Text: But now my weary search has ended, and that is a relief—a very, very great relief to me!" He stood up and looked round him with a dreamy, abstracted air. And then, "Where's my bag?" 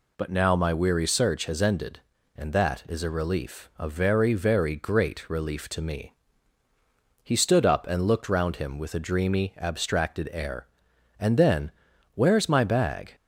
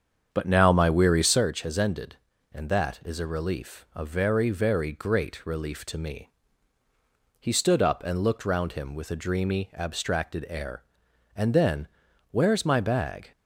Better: first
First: none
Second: starts louder than the rest; strong; until 1.5 s; 7.5 dB

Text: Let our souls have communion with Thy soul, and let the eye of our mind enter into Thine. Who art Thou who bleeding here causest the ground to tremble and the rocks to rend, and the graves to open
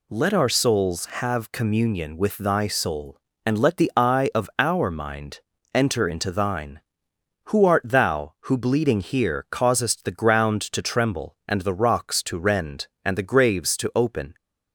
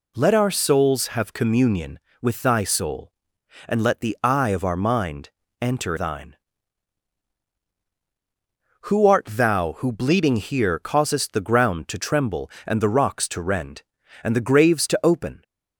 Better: first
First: pauses between "mind" and "enter"; slight; at 5.4 s; 0.34 s long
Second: pauses between "mind" and "enter"; slight; at 5.2 s; 0.32 s long // skips "into"; at 5.9 s

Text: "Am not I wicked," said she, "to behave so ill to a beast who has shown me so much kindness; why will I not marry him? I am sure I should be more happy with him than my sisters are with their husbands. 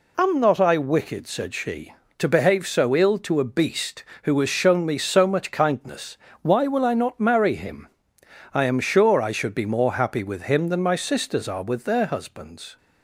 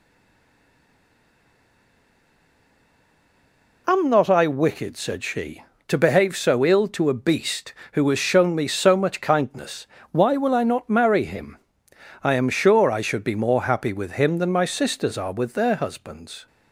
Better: first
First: none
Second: stays silent before the first word; strong; until 3.8 s; 3.8 s long

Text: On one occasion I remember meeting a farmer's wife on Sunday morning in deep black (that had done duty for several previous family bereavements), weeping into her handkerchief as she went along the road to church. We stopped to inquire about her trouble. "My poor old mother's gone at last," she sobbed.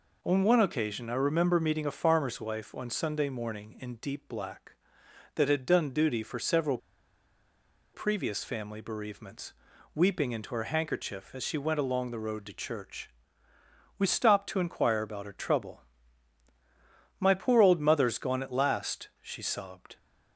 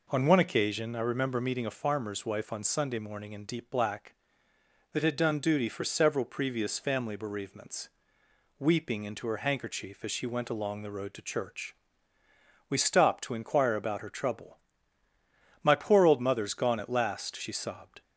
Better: second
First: pauses between "several" and "previous"; at 6.7 s; 1.1 s long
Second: none

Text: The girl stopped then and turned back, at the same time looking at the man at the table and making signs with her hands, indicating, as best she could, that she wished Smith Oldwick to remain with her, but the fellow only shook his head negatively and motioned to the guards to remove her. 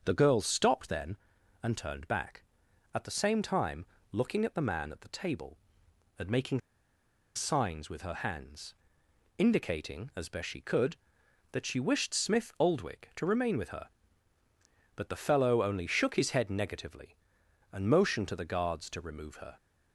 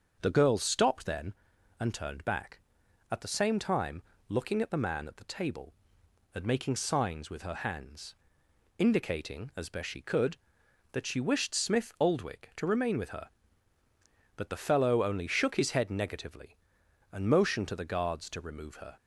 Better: second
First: starts louder than the rest; until 1.0 s; 6.5 dB // pauses between "time" and "looking"; slight; at 3.8 s; 0.26 s long // pauses between "making" and "signs"; noticeable; at 6.5 s; 0.76 s long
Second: starts louder than the rest; until 1.2 s; 6.5 dB // pauses between "time" and "looking"; slight; at 4.0 s; 0.26 s long

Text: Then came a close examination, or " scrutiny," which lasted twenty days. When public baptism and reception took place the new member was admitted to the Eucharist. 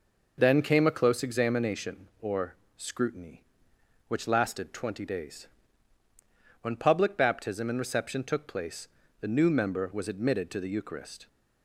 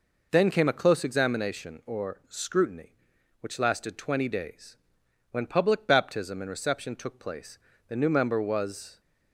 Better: first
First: pauses between "place" and "the"; slight; at 8.8 s; 0.34 s long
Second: pauses between "place" and "the"; slight; at 7.5 s; 0.30 s long // stops before "admitted to the Eucharist"; at 9.0 s

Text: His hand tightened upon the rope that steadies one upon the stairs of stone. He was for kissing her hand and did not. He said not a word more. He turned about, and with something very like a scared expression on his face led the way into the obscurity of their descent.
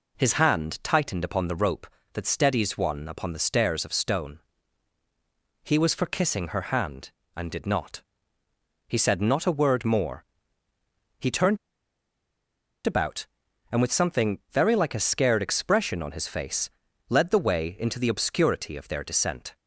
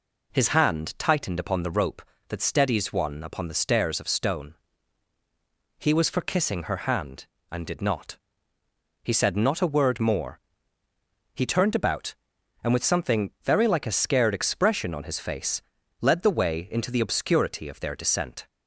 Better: second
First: pauses between "turned" and "about"; strong; at 11.5 s; 1.2 s long // pauses between "face" and "led"; at 16.6 s; 0.40 s long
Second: pauses between "face" and "led"; at 15.6 s; 0.40 s long

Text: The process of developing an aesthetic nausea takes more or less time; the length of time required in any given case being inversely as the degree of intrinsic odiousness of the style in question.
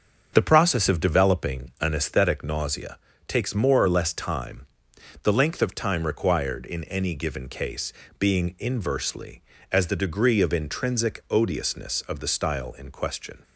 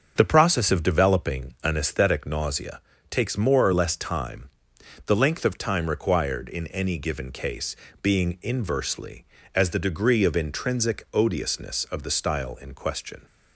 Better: neither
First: starts louder than the rest; until 1.3 s; 7 dB // pauses between "nausea" and "takes"; slight; at 2.9 s; 0.30 s long // pauses between "case" and "being"; slight; at 7.9 s; 0.26 s long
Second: starts louder than the rest; until 1.1 s; 7 dB // pauses between "nausea" and "takes"; slight; at 2.8 s; 0.30 s long // pauses between "case" and "being"; slight; at 7.7 s; 0.26 s long

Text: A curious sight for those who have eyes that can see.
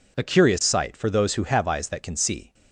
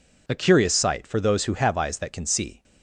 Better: neither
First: none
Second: none

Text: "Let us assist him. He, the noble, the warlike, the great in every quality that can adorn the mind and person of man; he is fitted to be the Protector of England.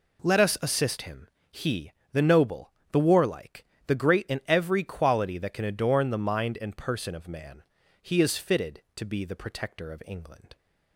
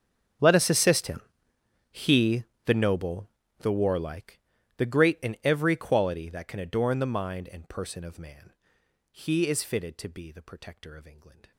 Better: first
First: none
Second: gets quieter; strong; throughout; 24.5 dB

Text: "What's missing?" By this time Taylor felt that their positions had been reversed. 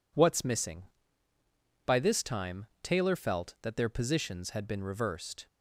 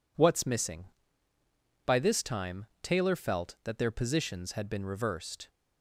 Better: neither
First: pauses between "time" and "Taylor"; slight; at 2.6 s; 0.16 s long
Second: pauses between "time" and "Taylor"; slight; at 2.6 s; 0.16 s long

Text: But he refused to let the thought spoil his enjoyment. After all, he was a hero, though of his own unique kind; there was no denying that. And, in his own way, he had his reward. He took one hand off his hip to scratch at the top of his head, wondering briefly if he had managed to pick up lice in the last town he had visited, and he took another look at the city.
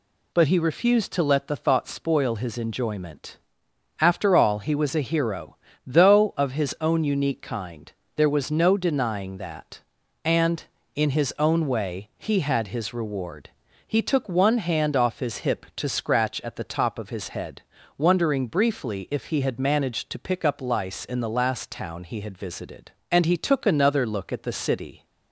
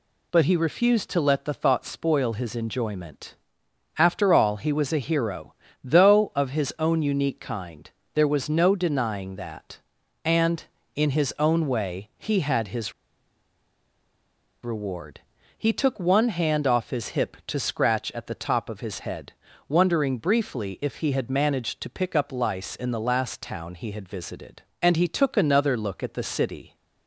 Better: first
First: none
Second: pauses between "his" and "reward"; strong; at 12.9 s; 1.7 s long

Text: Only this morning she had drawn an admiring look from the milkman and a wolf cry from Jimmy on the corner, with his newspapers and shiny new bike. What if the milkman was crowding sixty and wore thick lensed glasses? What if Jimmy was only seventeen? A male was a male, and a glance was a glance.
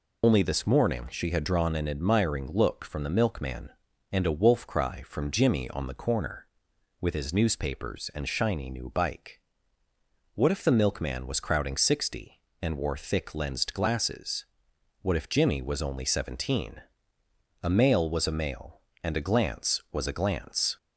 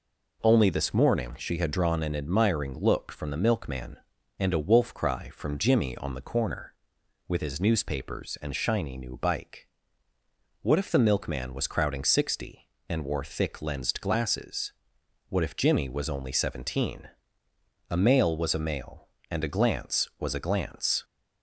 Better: second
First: loses the start of "Only"; at 0.2 s; 95 ms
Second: none

